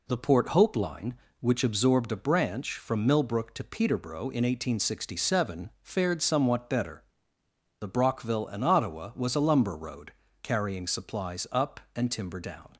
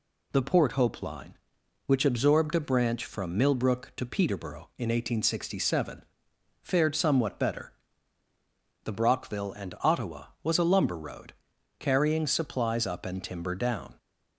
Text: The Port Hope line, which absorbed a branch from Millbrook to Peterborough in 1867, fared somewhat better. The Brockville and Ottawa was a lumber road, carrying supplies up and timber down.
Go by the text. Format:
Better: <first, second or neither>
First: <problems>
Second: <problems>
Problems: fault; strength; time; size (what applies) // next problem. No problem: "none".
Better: neither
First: none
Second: none